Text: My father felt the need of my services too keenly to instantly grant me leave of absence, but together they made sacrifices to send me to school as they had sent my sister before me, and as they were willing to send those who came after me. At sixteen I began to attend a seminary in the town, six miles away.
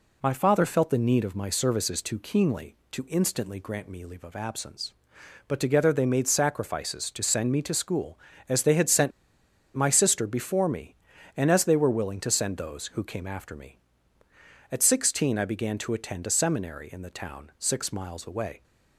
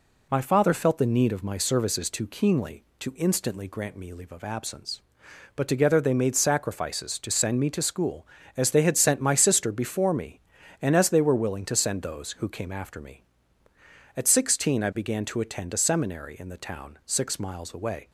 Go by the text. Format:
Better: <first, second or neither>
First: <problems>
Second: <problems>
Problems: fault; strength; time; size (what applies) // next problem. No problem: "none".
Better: second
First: pauses between "sent" and "my"; noticeable; at 9.1 s; 0.65 s long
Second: none